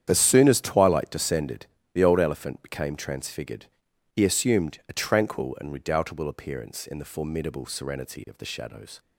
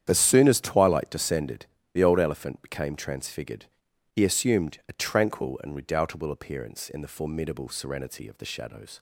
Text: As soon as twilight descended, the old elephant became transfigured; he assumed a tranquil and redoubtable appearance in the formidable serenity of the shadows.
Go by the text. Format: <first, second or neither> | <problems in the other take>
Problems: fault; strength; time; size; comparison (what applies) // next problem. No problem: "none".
neither | starts louder than the rest; strong; the same in both